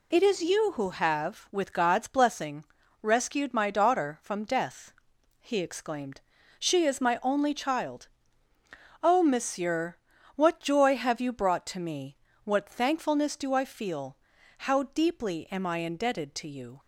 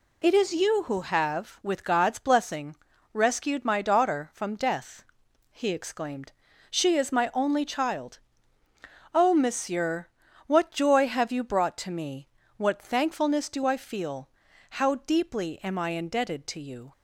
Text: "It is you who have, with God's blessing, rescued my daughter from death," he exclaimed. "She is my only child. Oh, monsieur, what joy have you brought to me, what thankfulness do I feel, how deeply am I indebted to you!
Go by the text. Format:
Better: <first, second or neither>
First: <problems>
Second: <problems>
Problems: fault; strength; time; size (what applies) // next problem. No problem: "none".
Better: neither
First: none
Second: none